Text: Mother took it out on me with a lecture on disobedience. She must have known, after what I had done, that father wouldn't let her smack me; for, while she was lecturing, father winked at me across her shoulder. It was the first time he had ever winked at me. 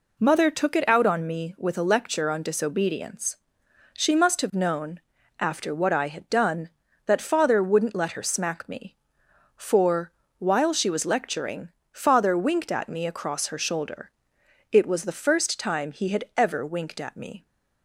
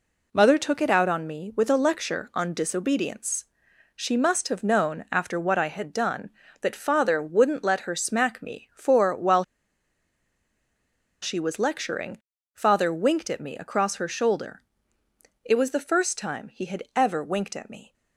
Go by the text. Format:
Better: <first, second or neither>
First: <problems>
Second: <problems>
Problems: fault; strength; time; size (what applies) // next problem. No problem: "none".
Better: first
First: none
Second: pauses between "while" and "she"; strong; at 9.4 s; 1.8 s long